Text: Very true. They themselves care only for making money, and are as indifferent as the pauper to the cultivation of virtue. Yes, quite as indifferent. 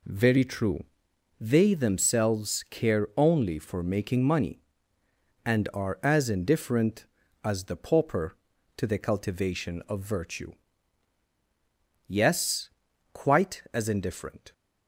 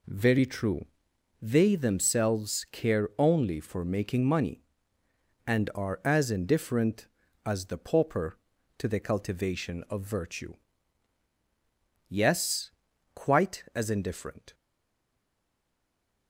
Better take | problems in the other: first | stays silent after the last word; noticeable; from 14.5 s on; 1.7 s long

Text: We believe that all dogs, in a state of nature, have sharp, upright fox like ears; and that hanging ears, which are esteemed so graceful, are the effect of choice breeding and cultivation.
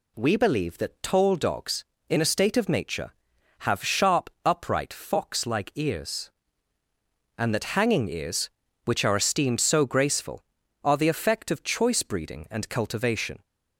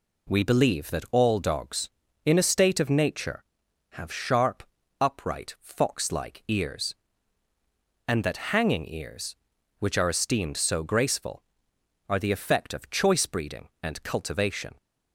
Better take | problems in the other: second | says "tall" for "all"; at 1.0 s

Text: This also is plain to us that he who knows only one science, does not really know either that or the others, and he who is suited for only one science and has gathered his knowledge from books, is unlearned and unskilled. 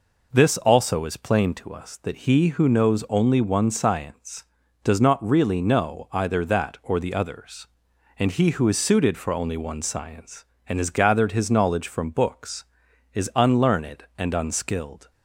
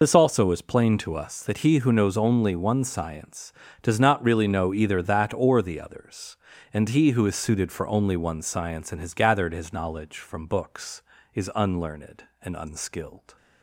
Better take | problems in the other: first | loses the start of "This"; at 0.0 s; 55 ms

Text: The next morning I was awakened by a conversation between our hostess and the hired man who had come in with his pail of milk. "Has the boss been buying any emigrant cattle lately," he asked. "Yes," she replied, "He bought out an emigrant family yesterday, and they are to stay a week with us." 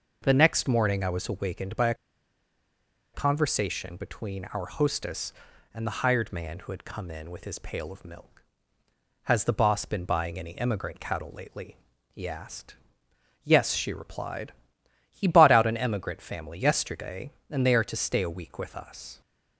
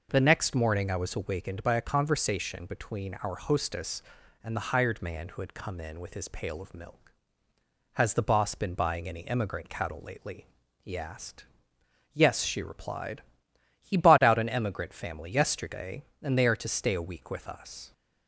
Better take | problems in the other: second | pauses between "a" and "conversation"; at 1.9 s; 1.1 s long

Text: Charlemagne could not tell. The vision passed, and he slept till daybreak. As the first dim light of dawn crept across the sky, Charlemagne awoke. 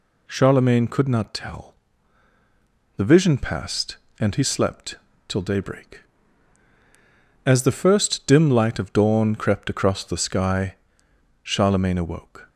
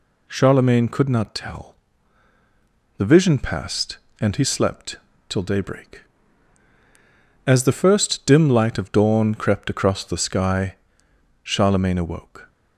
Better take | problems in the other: neither | pauses between "slept" and "till"; slight; the same in both

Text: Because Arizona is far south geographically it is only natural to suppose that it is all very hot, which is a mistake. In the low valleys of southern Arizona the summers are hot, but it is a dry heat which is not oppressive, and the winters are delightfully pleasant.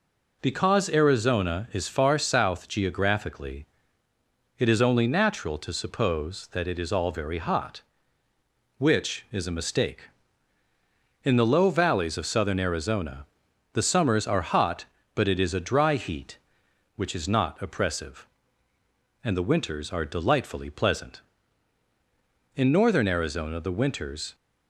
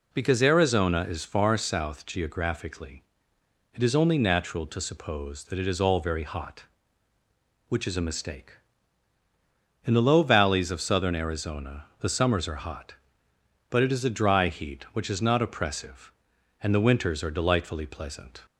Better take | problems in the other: second | pauses between "geographically" and "it"; noticeable; at 3.6 s; 0.92 s long; noticeable in the second // pauses between "Arizona" and "the"; noticeable; at 13.2 s; 0.48 s long; slight in the second // goes on to say "In northern Arizona the winters"; strong; from 22.5 s on; 1.8 s long

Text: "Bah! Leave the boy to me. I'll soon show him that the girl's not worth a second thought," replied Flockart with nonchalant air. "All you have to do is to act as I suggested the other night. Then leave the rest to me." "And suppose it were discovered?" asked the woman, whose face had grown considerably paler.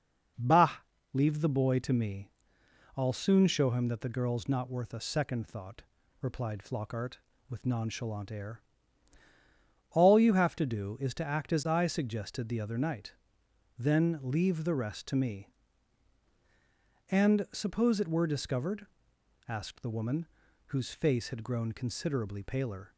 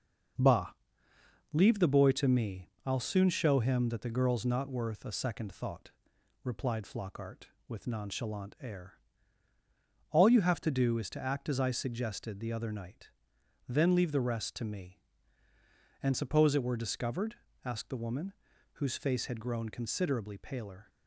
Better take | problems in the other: first | gets quieter; noticeable; throughout; 5.5 dB

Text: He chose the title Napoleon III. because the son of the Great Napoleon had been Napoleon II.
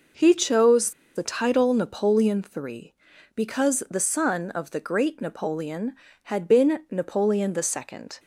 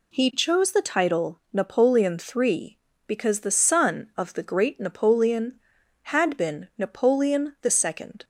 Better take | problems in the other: second | pauses between "chose" and "the"; slight; at 0.9 s; 0.23 s long

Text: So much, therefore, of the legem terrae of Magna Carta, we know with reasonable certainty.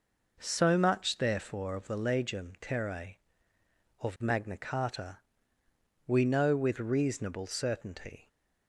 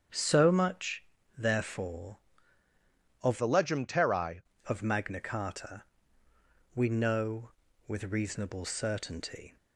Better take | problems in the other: first | starts louder than the rest; strong; until 1.4 s; 7.5 dB // changes voice from "the" to "terrae"; from 3.3 to 4.4 s; 1.1 s long

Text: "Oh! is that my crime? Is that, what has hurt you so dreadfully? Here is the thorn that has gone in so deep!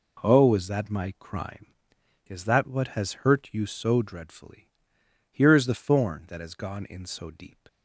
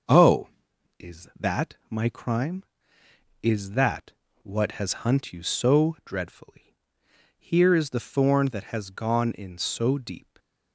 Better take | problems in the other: first | starts louder than the rest; until 1.7 s; 6.5 dB // pauses between "that" and "my"; slight; at 1.7 s; 0.16 s long // says "hunt" for "hurt"; at 5.0 s

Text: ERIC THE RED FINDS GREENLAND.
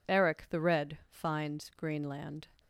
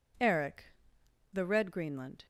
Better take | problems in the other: first | pauses between "ERIC" and "THE"; noticeable; at 0.7 s; 0.62 s long // skips "FINDS"; at 1.6 s

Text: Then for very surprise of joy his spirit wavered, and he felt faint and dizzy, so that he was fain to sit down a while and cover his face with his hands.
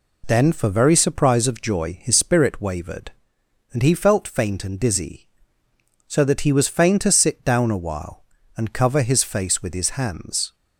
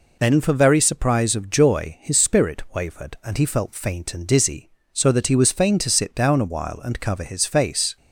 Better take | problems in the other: first | stops before "with his hands"; at 7.9 s

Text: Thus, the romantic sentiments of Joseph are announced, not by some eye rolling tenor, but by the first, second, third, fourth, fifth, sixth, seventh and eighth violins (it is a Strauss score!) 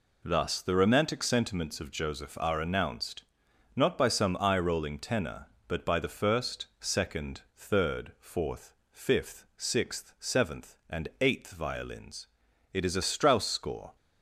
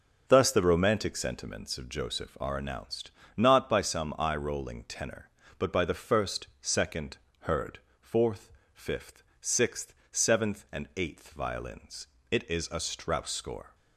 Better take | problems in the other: first | starts louder than the rest; until 1.2 s; 6.5 dB // says "heard" for "third"; at 7.4 s

